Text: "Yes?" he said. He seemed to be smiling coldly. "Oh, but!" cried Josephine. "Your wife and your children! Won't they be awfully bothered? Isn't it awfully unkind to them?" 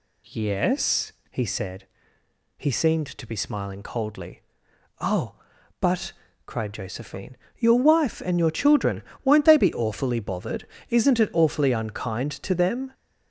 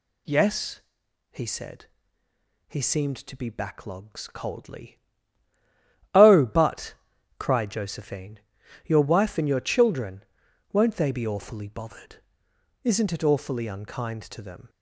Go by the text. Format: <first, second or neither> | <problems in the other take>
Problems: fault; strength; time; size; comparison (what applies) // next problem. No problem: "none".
first | says "backlogs" for "smiling"; at 3.5 s